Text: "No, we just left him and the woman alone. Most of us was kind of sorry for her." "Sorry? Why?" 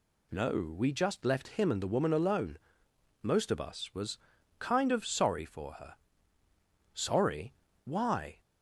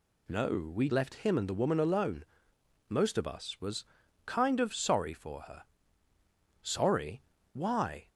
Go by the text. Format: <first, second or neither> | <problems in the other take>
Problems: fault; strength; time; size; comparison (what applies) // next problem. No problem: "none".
first | skips "just"; at 0.8 s // pauses between "was" and "kind"; at 3.8 s; 0.42 s long; also in the first